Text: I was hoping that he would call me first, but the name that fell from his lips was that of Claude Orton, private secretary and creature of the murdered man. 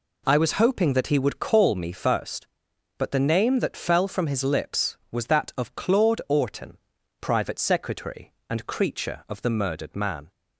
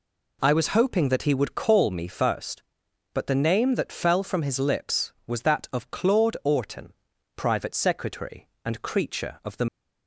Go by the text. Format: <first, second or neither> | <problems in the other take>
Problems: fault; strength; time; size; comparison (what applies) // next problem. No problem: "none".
first | stops before "murdered man"; at 9.6 s